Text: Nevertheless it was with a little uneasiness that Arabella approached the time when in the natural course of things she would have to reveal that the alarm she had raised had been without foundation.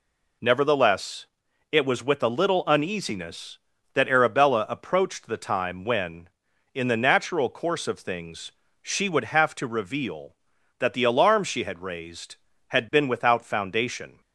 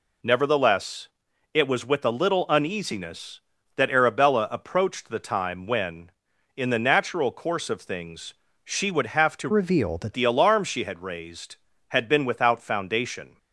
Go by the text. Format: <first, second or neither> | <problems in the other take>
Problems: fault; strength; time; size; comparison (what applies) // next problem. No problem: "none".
first | pauses between "Nevertheless" and "it"; noticeable; at 1.0 s; 0.46 s long; noticeable in the first // pauses between "things" and "she"; slight; at 8.3 s; 0.30 s long; slight in the first // changes voice from "reveal" to "that"; from 9.5 to 10.1 s; 0.6 s long